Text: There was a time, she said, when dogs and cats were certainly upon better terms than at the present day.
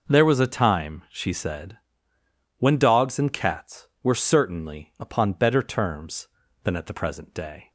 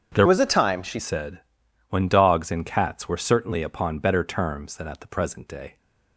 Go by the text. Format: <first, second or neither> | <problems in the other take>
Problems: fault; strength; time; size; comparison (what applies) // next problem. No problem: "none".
first | starts louder than the rest; strong; until 1.1 s; 7.5 dB // changes voice from "was" to "she"; from 0.2 to 0.9 s; 0.7 s long